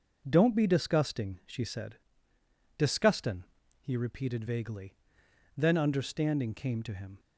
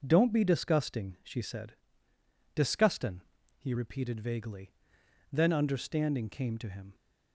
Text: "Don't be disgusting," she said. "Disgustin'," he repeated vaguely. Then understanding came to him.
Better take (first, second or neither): neither